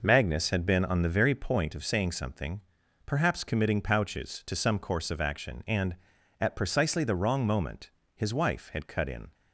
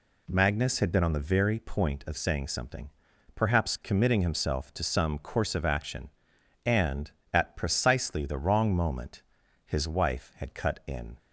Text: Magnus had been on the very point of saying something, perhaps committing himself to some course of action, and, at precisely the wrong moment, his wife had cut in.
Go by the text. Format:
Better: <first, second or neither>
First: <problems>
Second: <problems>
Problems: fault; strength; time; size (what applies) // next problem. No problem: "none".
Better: second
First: says "pouches" for "himself"; at 3.8 s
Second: none